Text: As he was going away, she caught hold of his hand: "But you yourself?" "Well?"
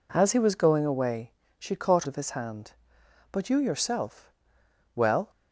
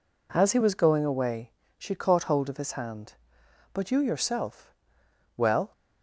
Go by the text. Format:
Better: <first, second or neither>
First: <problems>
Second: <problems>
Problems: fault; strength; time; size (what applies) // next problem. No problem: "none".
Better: second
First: skips "hold"; at 2.0 s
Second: none